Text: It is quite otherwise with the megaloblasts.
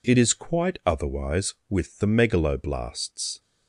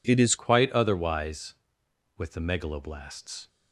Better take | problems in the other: first | changes voice at "quite"; from 0.3 s on; 3.1 s long

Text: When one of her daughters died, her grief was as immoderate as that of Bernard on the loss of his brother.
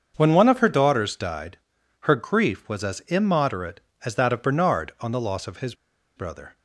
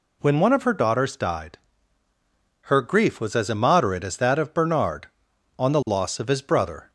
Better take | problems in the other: second | starts louder than the rest; until 1.1 s; 7 dB // pauses between "his" and "brother"; at 5.7 s; 0.41 s long

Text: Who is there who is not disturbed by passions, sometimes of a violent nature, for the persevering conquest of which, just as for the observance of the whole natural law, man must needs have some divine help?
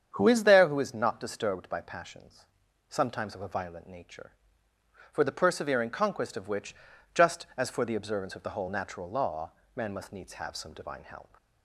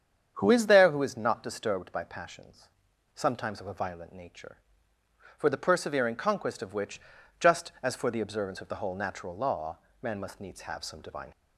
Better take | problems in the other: first | starts louder than the rest; strong; until 1.4 s; 8 dB; strong in the first // stops before "help"; at 11.3 s

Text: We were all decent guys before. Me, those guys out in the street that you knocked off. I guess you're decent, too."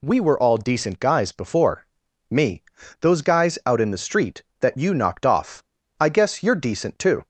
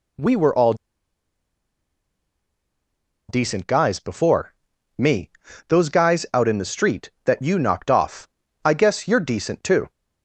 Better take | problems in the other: first | pauses between "all" and "decent"; strong; at 0.7 s; 2.5 s long

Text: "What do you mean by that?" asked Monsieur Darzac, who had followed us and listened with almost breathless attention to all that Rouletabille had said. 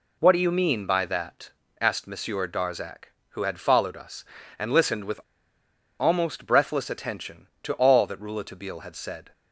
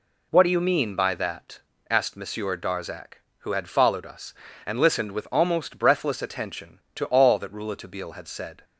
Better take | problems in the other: second | pauses between "with" and "almost"; noticeable; at 5.2 s; 0.78 s long

